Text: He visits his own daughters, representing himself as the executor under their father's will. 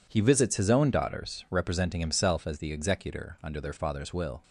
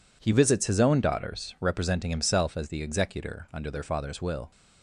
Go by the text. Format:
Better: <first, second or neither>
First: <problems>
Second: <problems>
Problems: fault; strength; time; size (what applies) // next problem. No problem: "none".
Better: neither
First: none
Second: none